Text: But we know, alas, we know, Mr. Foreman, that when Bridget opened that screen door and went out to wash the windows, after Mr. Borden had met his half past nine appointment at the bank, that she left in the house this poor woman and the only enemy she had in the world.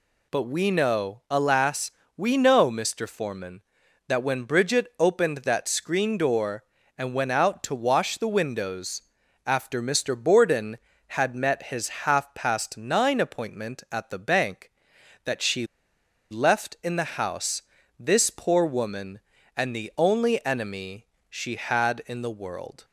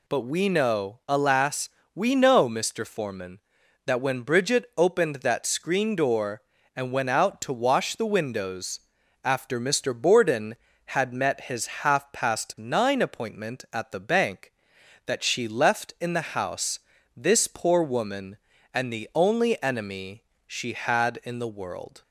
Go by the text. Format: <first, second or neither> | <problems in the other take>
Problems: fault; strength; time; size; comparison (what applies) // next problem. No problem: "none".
second | pauses between "his" and "half"; slight; at 11.8 s; 0.16 s long; slight in the second // pauses between "she" and "left"; noticeable; at 15.6 s; 0.64 s long // pauses between "house" and "this"; slight; at 17.6 s; 0.36 s long; slight in the second // pauses between "enemy" and "she"; slight; at 21.0 s; 0.24 s long; slight in the second